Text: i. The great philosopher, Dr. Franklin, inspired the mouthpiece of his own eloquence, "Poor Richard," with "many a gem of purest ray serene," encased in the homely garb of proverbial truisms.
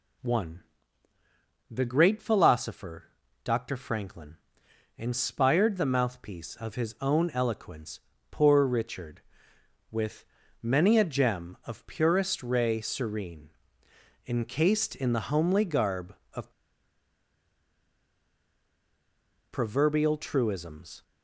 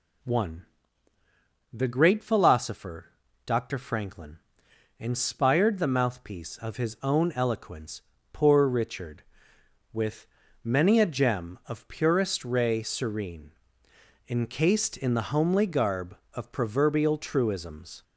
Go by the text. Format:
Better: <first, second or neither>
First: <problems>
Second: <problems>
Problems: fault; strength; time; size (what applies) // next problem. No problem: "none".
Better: second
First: pauses between "with" and "many"; slight; at 10.2 s; 0.36 s long // pauses between "of" and "proverbial"; strong; at 16.5 s; 3.0 s long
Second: pauses between "with" and "many"; slight; at 10.2 s; 0.36 s long